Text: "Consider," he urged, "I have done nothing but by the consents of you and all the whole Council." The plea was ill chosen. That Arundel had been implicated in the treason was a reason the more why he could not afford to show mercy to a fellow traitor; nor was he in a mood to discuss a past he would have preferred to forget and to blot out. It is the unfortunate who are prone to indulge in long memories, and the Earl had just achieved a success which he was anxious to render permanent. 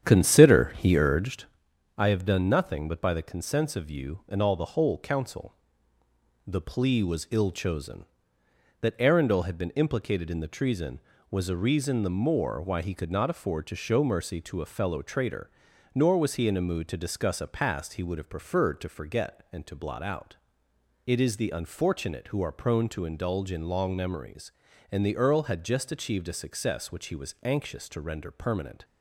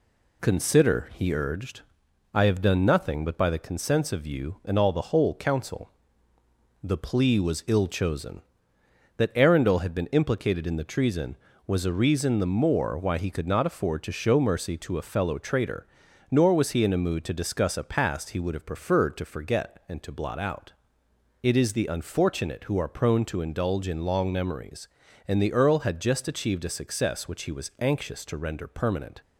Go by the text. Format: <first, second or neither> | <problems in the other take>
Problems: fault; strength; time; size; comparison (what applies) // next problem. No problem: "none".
second | starts louder than the rest; strong; until 1.6 s; 9 dB